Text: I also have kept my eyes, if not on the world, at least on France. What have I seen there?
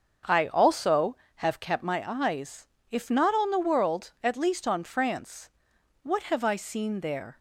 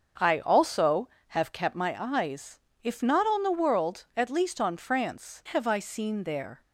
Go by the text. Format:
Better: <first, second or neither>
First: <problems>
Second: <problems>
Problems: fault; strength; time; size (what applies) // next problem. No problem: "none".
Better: first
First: starts louder than the rest; until 1.4 s; 6.5 dB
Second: starts louder than the rest; until 1.3 s; 6.5 dB // skips "What"; at 5.4 s